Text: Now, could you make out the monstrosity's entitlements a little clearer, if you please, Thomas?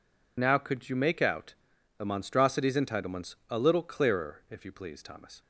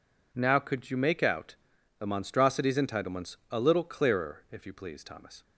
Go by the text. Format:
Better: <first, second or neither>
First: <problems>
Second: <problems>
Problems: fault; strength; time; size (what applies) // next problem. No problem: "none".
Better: second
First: loses the start of "Now"; at 0.3 s; 45 ms // pauses between "out" and "the"; at 1.5 s; 0.42 s long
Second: pauses between "out" and "the"; at 1.5 s; 0.42 s long